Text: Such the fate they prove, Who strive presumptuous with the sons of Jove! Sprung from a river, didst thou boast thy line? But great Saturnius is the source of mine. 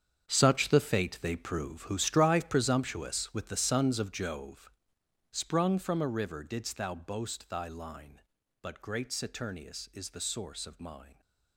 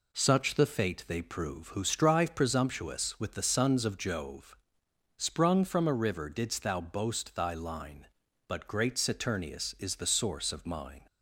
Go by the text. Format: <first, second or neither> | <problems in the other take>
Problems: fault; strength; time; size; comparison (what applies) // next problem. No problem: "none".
second | gets quieter; strong; throughout; 14 dB